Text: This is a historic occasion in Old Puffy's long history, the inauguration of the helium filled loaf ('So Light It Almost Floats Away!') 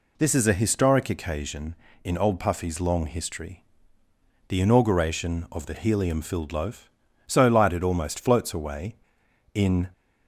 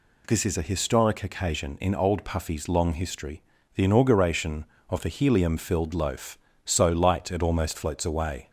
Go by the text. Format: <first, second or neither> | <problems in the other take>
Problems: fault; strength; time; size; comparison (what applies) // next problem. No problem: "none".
second | goes on to say "in"; slight; from 9.5 s on; 0.36 s long